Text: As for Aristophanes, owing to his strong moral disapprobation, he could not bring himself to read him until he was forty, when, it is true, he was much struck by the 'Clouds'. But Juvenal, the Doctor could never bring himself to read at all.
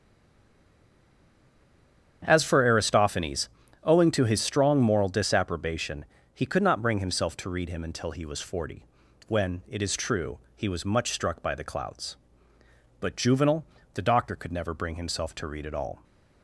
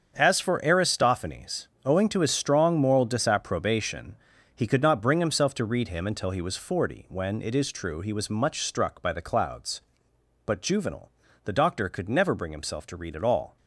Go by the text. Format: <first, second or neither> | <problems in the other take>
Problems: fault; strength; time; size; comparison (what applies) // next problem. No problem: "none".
second | stays silent before the first word; until 2.2 s; 2.2 s long // starts louder than the rest; strong; until 3.2 s; 8.5 dB; strong in the second